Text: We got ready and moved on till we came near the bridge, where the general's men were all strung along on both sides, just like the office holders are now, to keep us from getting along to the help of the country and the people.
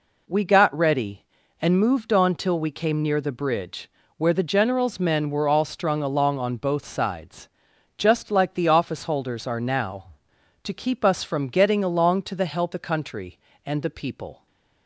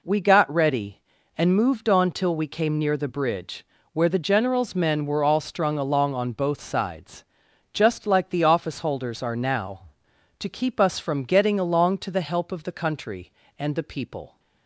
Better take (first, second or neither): second